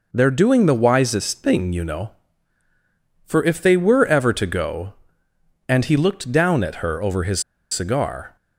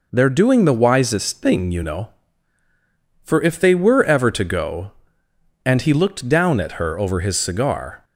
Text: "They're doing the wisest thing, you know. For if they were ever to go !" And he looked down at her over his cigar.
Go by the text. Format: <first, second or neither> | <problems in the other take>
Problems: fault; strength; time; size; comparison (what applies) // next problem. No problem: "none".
second | pauses between "his" and "cigar"; slight; at 7.4 s; 0.30 s long